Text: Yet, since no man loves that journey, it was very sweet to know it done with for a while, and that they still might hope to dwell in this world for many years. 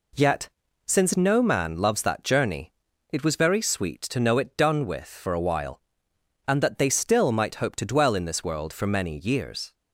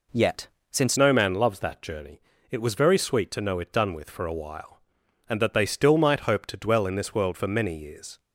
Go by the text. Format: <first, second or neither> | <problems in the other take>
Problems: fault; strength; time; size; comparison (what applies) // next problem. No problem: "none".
first | changes voice at "no"; from 0.9 s on; 7.2 s long